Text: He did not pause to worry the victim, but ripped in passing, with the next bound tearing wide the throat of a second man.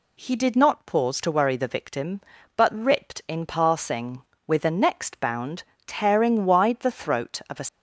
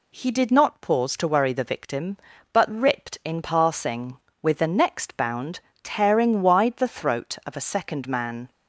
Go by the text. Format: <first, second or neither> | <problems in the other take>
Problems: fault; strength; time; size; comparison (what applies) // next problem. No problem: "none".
second | pauses between "bound" and "tearing"; slight; at 5.6 s; 0.22 s long; slight in the second // stops before "second man"; at 7.6 s